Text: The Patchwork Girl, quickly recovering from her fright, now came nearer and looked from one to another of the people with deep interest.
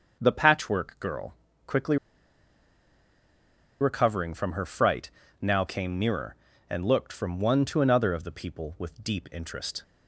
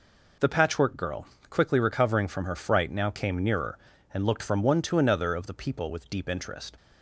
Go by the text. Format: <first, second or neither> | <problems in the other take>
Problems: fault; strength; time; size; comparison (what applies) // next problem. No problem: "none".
second | starts louder than the rest; until 1.2 s; 6.5 dB // pauses between "quickly" and "recovering"; strong; at 1.9 s; 1.8 s long